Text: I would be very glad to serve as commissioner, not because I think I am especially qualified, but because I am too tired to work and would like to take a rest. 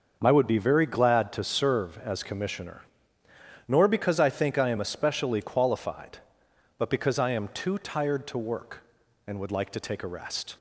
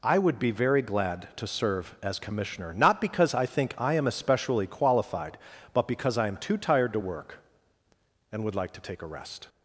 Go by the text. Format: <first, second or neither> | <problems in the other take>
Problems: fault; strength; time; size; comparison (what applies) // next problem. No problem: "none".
second | starts louder than the rest; until 1.2 s; 6 dB // says "nor" for "not"; at 3.6 s